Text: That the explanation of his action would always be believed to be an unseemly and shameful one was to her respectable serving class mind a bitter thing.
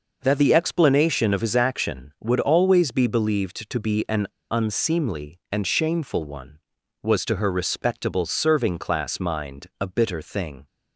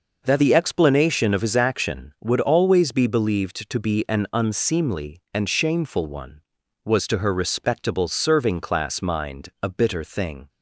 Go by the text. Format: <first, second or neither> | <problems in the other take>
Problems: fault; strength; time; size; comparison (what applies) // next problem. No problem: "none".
second | pauses between "an" and "unseemly"; slight; at 4.2 s; 0.25 s long